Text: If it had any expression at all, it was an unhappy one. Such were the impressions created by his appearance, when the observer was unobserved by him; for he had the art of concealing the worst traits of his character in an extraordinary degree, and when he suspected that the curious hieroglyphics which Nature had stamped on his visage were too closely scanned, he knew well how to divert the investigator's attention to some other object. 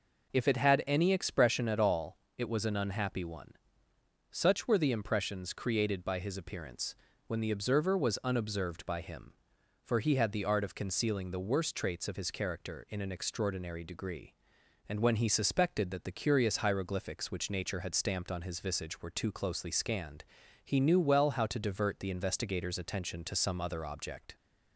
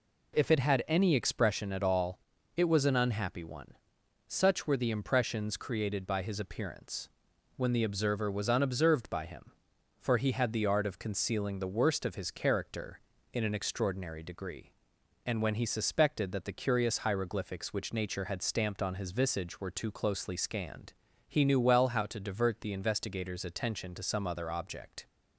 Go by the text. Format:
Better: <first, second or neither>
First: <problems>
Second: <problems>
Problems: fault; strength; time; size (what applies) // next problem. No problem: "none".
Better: first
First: none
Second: skips "traits"; at 12.0 s